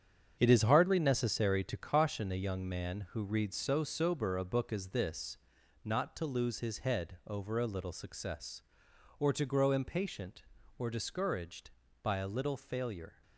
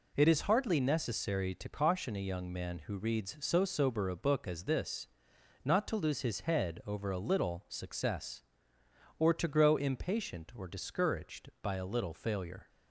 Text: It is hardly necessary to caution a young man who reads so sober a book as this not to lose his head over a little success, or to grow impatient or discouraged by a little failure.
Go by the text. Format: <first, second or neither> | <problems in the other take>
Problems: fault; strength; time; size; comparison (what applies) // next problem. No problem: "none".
second | gets quieter; strong; throughout; 9 dB // pauses between "this" and "not"; noticeable; at 5.3 s; 0.46 s long; noticeable in the second